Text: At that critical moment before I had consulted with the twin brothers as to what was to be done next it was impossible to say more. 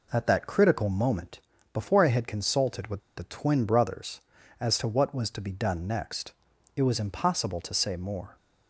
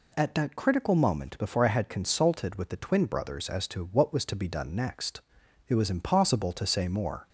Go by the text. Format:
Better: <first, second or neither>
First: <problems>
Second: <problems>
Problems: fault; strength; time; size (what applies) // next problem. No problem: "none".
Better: second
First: pauses between "moment" and "before"; slight; at 1.4 s; 0.34 s long // pauses between "with" and "the"; slight; at 3.0 s; 0.16 s long // pauses between "next" and "it"; at 6.3 s; 0.44 s long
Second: pauses between "next" and "it"; noticeable; at 5.2 s; 0.48 s long